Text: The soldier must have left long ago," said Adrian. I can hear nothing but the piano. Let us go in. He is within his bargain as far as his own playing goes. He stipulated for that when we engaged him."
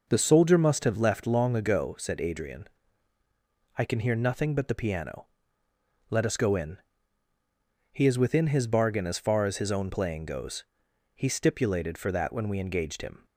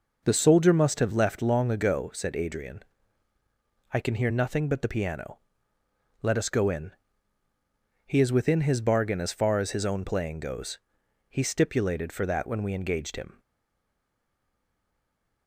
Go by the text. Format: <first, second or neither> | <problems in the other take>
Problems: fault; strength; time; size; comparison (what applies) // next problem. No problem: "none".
first | stays silent after the last word; from 13.3 s on; 2.1 s long